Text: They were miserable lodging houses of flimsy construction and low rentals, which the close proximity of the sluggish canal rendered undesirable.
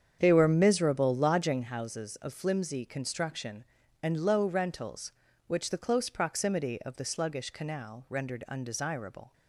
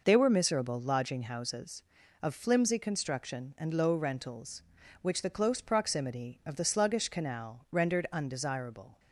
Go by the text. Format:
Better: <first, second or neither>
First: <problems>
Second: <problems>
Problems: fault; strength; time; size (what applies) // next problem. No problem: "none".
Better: second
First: starts louder than the rest; strong; until 1.7 s; 8 dB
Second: none